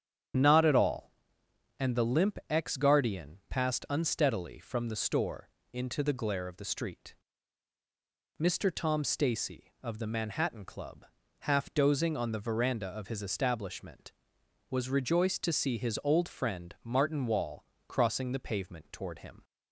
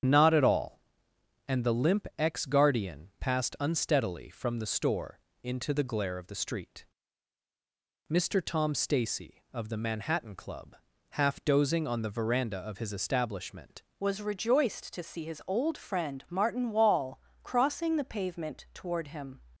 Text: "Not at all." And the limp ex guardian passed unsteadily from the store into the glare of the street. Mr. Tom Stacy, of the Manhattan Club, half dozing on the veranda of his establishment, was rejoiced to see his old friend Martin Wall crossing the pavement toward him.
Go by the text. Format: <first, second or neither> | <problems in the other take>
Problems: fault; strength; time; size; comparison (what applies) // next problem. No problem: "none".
first | starts louder than the rest; strong; until 1.7 s; 8 dB; strong in the first // pauses between "store" and "into"; slight; at 5.1 s; 0.24 s long; slight in the first // changes voice at "was"; from 14.0 s on; 5.4 s long // pauses between "Wall" and "crossing"; slight; at 17.2 s; 0.24 s long; slight in the first